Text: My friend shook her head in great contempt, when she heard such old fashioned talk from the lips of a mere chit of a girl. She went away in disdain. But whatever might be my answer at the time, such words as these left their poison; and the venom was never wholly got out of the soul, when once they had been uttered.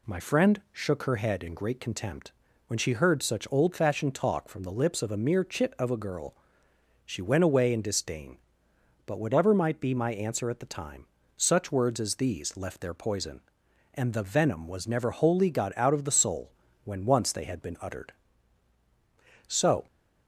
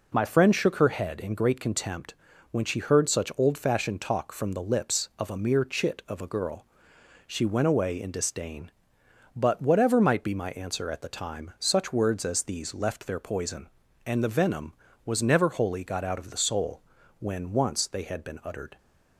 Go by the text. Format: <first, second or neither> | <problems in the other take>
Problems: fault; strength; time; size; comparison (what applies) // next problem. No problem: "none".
second | goes on to say "So"; slight; from 19.4 s on; 0.38 s long